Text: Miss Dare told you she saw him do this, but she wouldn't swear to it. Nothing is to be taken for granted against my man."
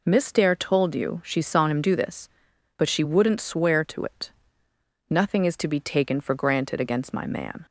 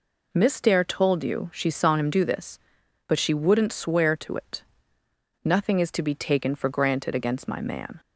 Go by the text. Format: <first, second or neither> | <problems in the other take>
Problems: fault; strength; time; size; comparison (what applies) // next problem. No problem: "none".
neither | none